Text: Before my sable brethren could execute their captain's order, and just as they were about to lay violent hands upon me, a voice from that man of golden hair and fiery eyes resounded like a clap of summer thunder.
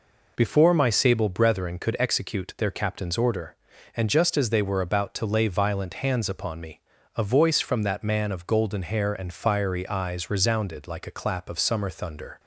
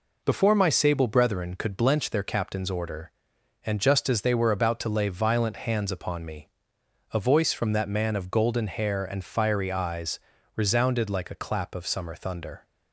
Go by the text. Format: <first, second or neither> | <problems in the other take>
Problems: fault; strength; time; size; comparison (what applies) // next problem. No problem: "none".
first | says "blench" for "execute"; at 1.7 s // pauses between "eyes" and "resounded"; slight; at 10.2 s; 0.34 s long